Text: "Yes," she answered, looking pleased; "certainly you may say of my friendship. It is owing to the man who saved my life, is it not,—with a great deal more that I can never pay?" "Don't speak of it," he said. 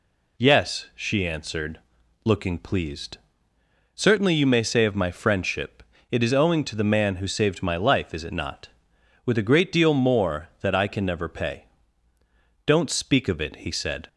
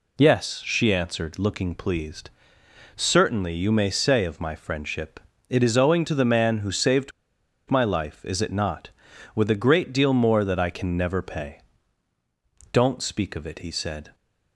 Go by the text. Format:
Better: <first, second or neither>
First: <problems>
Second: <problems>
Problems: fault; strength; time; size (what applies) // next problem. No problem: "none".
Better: first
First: none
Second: pauses between "saved" and "my"; noticeable; at 7.1 s; 0.58 s long